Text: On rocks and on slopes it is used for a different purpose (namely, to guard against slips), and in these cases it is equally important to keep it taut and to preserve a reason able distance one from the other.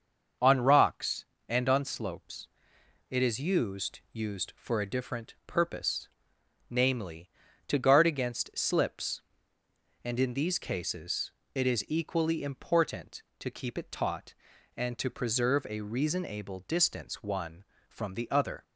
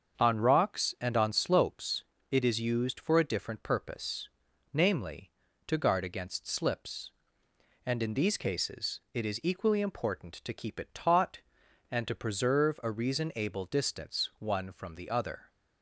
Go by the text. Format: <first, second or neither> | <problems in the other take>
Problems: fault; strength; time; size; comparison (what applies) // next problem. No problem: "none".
second | starts louder than the rest; until 1.6 s; 6.5 dB; also in the second // pauses between "slopes" and "it"; noticeable; at 2.4 s; 0.62 s long; slight in the second // says "used" twice; at 4.1 s // pauses between "cases" and "it"; slight; at 11.3 s; 0.24 s long; slight in the second